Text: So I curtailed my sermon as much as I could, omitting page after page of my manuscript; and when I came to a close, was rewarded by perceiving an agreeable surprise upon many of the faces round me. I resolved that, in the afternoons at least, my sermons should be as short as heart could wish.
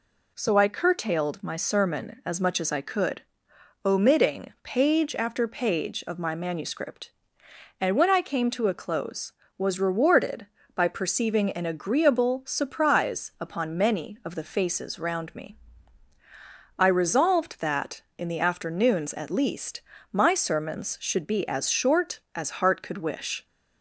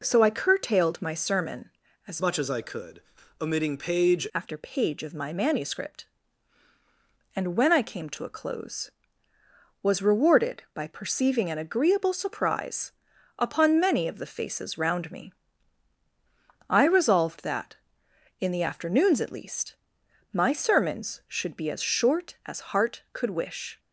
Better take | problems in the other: first | changes voice from "much" to "page"; from 2.2 to 4.2 s; 2.0 s long // pauses between "surprise" and "upon"; noticeable; at 12.9 s; 0.46 s long

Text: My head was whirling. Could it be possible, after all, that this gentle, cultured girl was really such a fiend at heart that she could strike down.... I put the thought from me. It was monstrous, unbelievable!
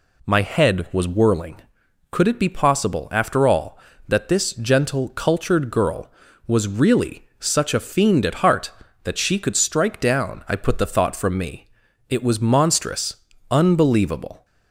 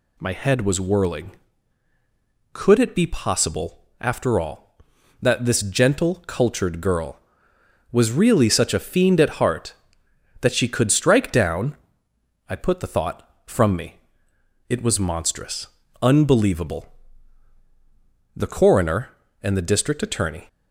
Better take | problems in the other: first | goes on to say "The coroner and the district attorney"; strong; from 18.3 s on; 2.1 s long

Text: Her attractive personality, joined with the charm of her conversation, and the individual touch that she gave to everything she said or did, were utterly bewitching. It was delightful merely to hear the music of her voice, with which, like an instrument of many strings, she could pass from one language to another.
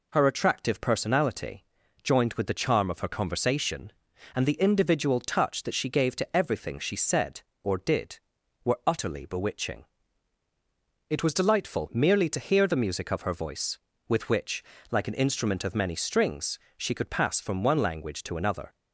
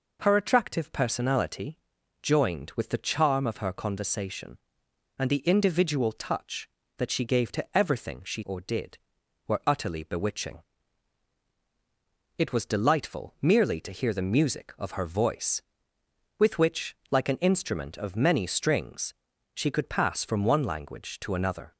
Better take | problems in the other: first | skips "said"; at 8.4 s

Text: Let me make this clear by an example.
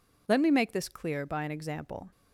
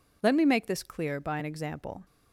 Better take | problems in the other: neither | none

